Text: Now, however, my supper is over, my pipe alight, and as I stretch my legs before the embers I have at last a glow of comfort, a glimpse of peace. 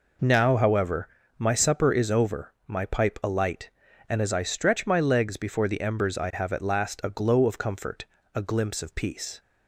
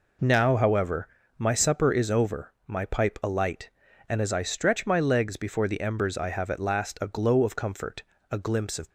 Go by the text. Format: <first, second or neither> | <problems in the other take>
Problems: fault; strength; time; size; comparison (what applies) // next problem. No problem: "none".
first | stops before "peace"; at 8.8 s